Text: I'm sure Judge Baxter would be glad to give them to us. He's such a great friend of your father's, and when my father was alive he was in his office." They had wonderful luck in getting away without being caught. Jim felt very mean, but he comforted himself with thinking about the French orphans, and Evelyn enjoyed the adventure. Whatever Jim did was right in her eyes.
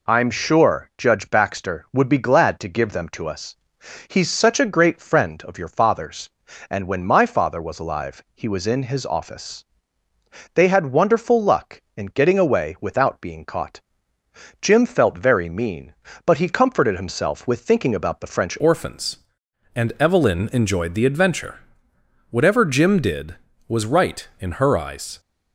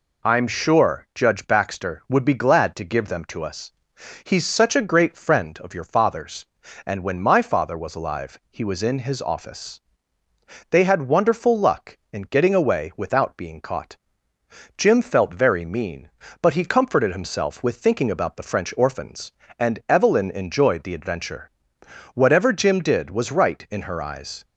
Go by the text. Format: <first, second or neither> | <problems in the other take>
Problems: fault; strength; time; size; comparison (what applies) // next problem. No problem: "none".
second | changes voice at "orphans"; from 18.5 s on; 6.6 s long